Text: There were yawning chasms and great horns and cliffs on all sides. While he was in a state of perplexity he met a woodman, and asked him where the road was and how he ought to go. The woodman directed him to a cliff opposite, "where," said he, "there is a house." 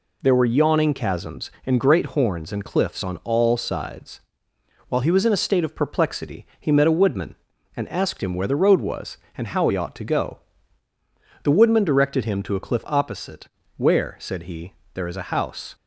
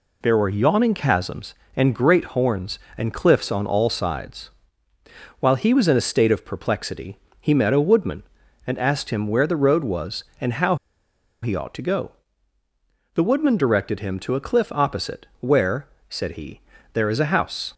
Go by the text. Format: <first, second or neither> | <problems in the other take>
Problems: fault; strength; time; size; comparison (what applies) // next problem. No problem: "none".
first | pauses between "perplexity" and "he"; slight; at 7.1 s; 0.26 s long // pauses between "how" and "he"; noticeable; at 10.7 s; 0.67 s long